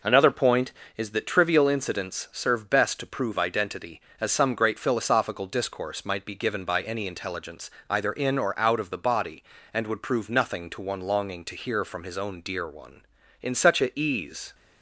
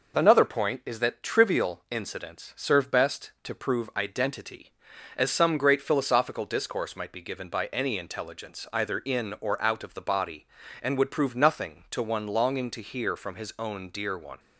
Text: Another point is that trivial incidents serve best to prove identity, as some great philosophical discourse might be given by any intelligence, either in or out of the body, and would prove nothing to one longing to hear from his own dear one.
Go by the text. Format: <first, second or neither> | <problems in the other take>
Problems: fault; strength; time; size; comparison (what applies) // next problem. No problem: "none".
second | goes on to say "In such a ease"; noticeable; from 13.4 s on; 1.1 s long